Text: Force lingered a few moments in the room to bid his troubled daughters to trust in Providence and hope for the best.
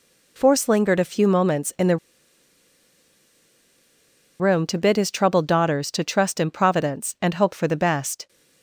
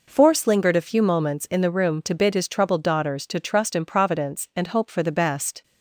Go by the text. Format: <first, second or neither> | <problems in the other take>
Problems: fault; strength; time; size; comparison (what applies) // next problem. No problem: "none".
second | pauses between "the" and "room"; strong; at 1.9 s; 2.4 s long